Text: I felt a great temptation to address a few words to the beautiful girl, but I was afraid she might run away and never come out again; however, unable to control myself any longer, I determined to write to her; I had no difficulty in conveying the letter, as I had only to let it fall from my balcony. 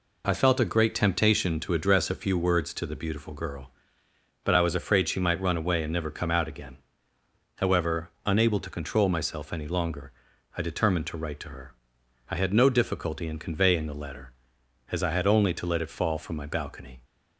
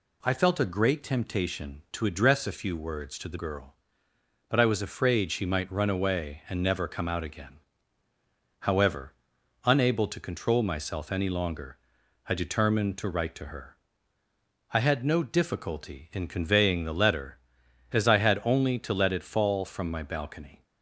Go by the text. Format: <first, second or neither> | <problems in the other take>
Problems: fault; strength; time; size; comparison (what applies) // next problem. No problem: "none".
first | skips "beautiful"; at 3.3 s